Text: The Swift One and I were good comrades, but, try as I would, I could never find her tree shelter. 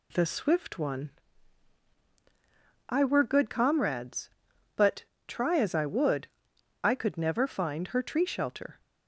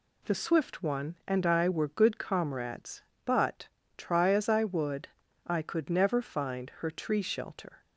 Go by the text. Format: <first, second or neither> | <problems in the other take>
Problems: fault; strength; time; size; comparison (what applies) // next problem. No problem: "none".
second | skips "and"; at 1.9 s